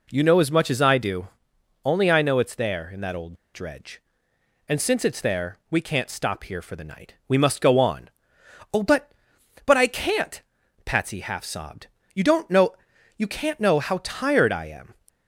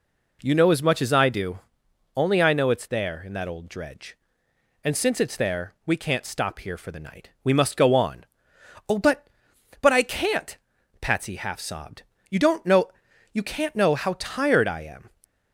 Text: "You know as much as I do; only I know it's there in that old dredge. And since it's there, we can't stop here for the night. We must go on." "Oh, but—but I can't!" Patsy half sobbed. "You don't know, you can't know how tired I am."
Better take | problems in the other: second | pauses between "old" and "dredge"; slight; at 3.3 s; 0.19 s long

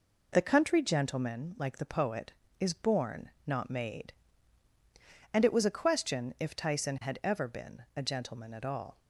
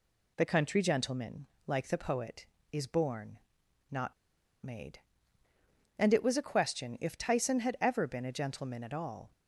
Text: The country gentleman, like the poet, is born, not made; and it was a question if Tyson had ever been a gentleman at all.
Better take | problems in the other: first | pauses between "not" and "made"; noticeable; at 4.1 s; 0.52 s long

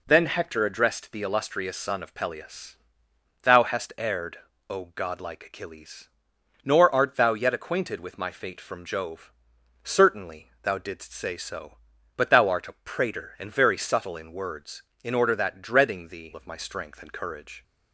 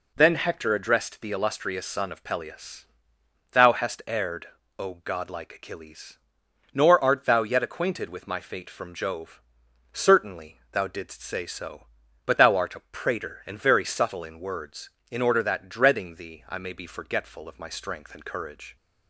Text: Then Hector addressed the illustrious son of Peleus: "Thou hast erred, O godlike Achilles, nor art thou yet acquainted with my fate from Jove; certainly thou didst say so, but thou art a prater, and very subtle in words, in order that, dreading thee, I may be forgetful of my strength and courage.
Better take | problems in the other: second | skips "I may be forgetful"; at 16.3 s

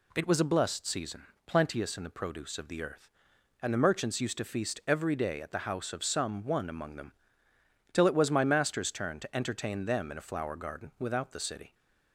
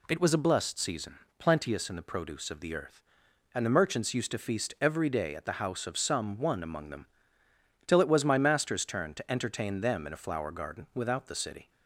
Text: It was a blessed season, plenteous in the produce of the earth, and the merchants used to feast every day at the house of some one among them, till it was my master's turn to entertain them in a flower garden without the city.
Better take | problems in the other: neither | none

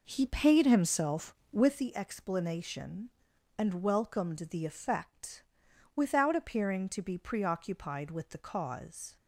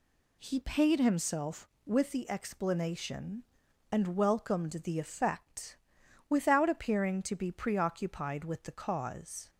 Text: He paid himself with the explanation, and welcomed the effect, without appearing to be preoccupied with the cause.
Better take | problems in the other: second | starts louder than the rest; noticeable; until 2.0 s; 5 dB

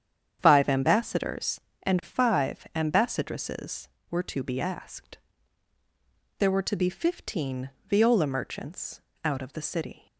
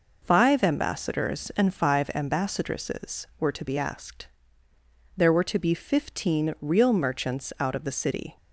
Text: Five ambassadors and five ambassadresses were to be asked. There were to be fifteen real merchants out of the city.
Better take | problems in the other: second | starts louder than the rest; strong; until 1.4 s; 8.5 dB // says "viola" for "real"; at 7.8 s // pauses between "merchants" and "out"; slight; at 9.0 s; 0.24 s long

